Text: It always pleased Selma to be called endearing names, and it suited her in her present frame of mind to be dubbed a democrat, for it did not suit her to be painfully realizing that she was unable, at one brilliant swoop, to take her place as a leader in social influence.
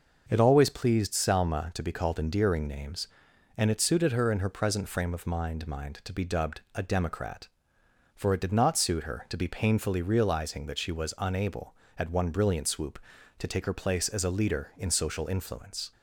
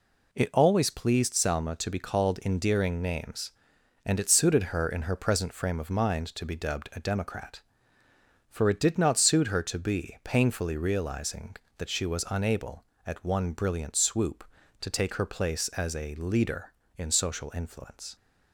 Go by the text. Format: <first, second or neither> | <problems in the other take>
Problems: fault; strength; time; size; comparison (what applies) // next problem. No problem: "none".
second | says "mind" twice; at 5.6 s // pauses between "dubbed" and "a"; slight; at 6.5 s; 0.16 s long